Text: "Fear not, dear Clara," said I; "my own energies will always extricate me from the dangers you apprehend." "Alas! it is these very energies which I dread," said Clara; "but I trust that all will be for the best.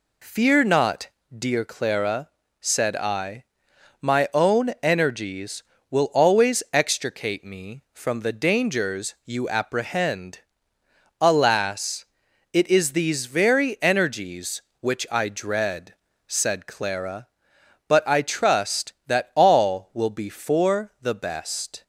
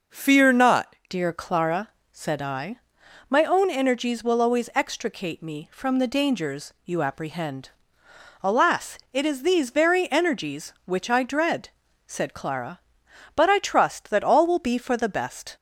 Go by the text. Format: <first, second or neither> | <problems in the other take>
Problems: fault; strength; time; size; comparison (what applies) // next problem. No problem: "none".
first | changes voice at "dear"; from 1.0 s on; 14.5 s long